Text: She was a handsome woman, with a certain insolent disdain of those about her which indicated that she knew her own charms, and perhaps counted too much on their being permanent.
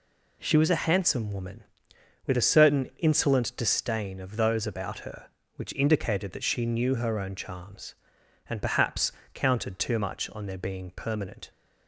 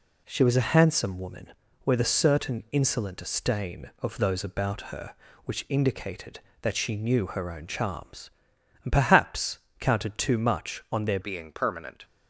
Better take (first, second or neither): first